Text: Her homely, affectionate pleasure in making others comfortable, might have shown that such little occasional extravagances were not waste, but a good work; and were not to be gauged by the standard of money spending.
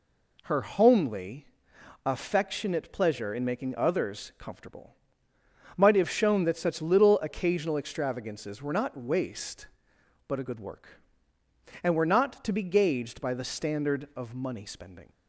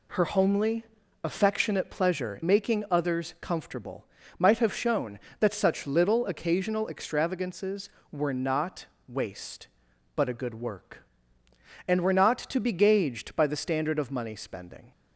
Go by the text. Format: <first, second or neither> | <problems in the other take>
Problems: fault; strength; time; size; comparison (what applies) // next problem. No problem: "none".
first | skips "in"; at 2.4 s // pauses between "not" and "waste"; slight; at 8.8 s; 0.22 s long